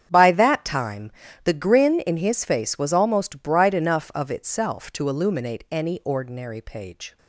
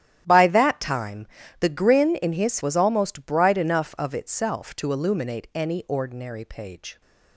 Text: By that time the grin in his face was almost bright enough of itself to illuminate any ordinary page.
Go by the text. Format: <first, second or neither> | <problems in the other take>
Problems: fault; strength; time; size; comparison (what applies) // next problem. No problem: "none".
first | starts louder than the rest; strong; until 1.2 s; 11 dB; strong in the first // pauses between "time" and "the"; slight; at 1.2 s; 0.32 s long; slight in the first // skips "face"; at 2.6 s